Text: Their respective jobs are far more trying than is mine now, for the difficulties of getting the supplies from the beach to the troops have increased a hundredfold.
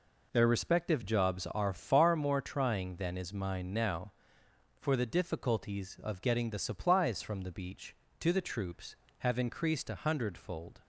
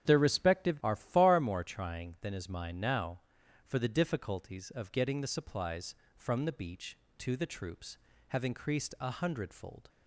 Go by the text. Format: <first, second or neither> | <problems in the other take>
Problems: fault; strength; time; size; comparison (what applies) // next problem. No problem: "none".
first | starts louder than the rest; strong; until 1.1 s; 9 dB // skips "jobs"; at 0.8 s